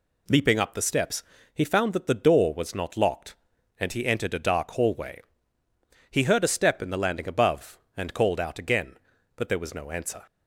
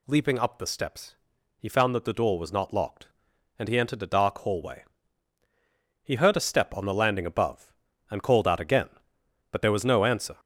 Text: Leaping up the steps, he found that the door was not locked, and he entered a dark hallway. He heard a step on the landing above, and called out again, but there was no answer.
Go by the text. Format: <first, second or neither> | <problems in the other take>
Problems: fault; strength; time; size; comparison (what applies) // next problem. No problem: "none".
second | says "in" for "on"; at 6.8 s